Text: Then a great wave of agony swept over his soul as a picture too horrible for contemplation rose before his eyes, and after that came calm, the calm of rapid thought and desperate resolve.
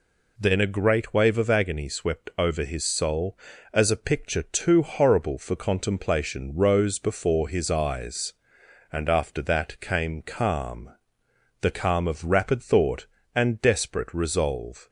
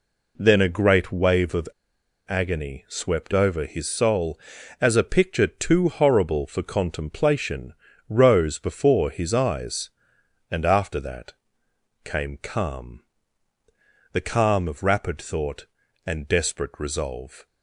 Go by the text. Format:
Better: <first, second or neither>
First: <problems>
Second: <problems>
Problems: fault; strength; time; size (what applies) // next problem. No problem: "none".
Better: first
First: none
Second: pauses between "of" and "agony"; noticeable; at 1.6 s; 0.59 s long // pauses between "contemplation" and "rose"; slight; at 7.7 s; 0.34 s long // pauses between "that" and "came"; noticeable; at 11.3 s; 0.70 s long